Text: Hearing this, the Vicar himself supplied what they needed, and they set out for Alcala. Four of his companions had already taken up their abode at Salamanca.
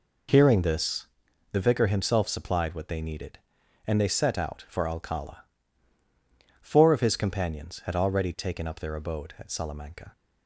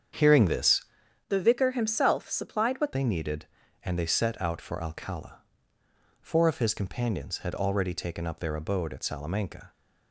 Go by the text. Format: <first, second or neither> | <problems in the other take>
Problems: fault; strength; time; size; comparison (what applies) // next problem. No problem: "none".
first | starts louder than the rest; strong; until 1.6 s; 7.5 dB // changes voice from "the" to "what"; from 1.2 to 2.9 s; 1.7 s long